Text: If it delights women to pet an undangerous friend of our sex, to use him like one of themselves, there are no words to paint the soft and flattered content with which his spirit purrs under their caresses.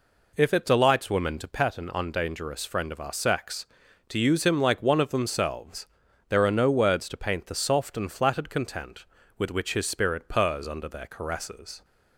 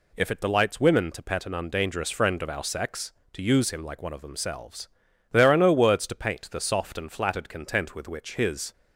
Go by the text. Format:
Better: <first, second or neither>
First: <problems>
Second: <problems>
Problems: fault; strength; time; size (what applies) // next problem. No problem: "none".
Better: first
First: none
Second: stops before "spirit purrs under their caresses"; at 8.7 s